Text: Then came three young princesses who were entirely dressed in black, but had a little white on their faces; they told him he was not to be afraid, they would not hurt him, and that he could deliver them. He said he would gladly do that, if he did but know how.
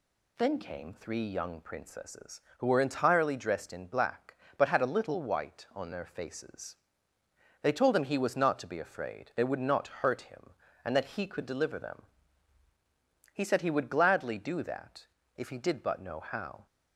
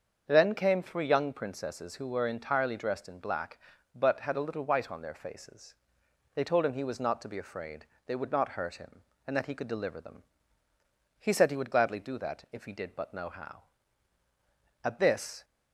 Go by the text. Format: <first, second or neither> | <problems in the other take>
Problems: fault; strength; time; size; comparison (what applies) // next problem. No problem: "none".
first | starts louder than the rest; until 1.2 s; 7 dB // goes on to say "At this"; from 14.8 s on; 0.60 s long